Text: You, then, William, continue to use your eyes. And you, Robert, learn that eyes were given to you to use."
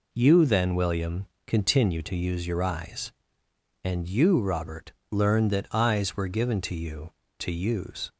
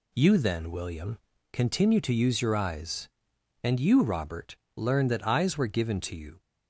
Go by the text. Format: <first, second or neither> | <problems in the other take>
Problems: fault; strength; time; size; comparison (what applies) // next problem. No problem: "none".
first | stops before "to use"; at 6.4 s